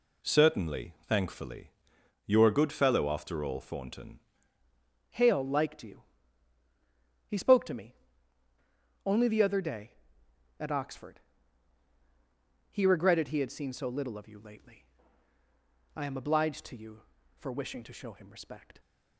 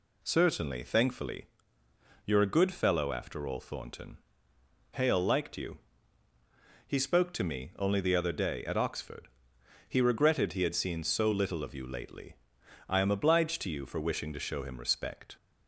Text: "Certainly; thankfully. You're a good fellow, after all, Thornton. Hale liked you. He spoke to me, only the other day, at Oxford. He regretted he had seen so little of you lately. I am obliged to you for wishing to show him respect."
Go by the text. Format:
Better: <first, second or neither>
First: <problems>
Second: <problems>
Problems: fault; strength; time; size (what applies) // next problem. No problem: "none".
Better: second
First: changes voice at "Hale"; from 5.0 s on; 13.7 s long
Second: none